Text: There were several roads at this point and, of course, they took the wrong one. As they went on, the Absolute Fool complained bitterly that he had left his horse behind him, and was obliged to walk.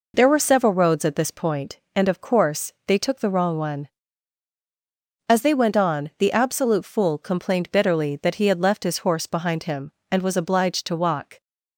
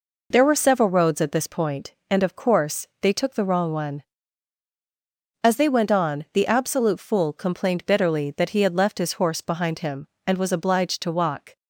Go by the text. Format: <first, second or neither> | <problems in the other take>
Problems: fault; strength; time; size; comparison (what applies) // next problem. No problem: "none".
neither | none